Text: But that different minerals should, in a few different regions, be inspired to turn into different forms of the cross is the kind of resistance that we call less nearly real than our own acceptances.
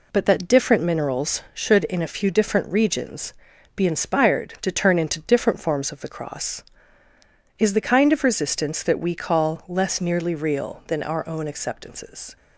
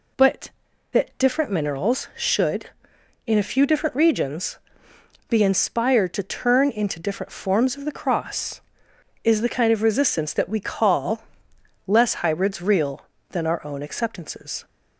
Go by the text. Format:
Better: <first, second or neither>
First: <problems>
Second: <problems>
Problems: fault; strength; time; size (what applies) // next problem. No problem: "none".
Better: first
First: none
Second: pauses between "call" and "less"; noticeable; at 11.2 s; 0.64 s long // says "hybrids" for "nearly"; at 12.1 s